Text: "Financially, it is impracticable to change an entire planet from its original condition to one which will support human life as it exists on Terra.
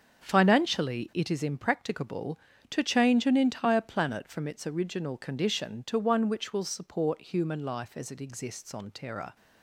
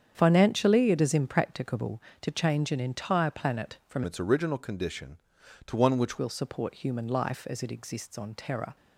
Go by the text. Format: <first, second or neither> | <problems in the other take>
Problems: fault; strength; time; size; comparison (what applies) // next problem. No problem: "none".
first | starts louder than the rest; strong; until 1.1 s; 8 dB; also in the first // changes voice from "its" to "which"; from 4.0 to 6.1 s; 2.1 s long